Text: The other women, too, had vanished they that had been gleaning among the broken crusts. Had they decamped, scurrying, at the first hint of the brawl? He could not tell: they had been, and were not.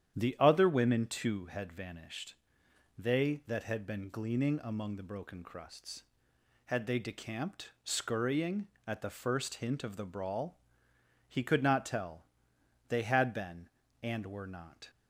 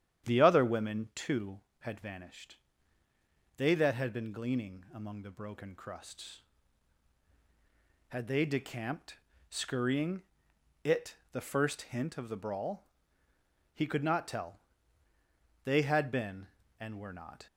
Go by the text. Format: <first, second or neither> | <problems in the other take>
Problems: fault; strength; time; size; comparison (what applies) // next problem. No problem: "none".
first | starts louder than the rest; strong; until 1.3 s; 10 dB; strong in the first // pauses between "vanished" and "they"; at 2.5 s; 1.0 s long; noticeable in the first // says "it" for "at"; at 10.8 s